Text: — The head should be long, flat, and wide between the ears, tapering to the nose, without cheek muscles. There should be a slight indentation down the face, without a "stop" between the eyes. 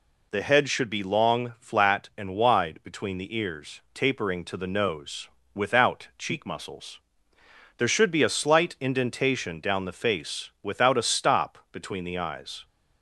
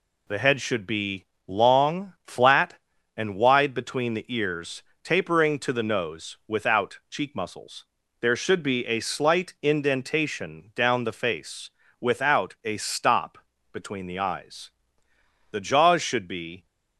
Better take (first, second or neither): first